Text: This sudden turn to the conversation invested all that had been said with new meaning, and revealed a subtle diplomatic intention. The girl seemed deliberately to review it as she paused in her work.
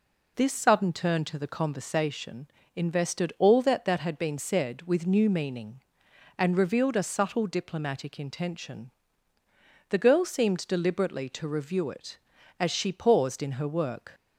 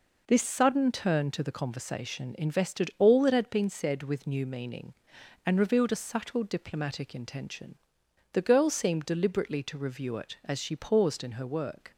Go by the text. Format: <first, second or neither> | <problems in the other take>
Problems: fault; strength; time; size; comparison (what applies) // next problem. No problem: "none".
second | pauses between "conversation" and "invested"; slight; at 2.4 s; 0.26 s long // says "that" twice; at 3.8 s